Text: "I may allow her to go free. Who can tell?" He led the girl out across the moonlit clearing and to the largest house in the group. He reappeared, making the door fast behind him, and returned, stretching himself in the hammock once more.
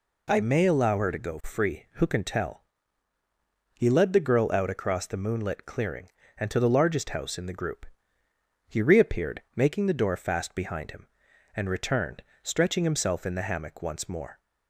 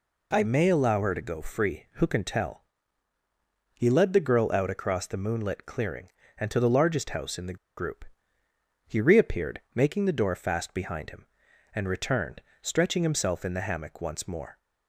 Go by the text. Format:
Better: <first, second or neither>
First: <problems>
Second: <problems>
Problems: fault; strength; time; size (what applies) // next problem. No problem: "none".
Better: first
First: none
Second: pauses between "the" and "group"; slight; at 7.5 s; 0.20 s long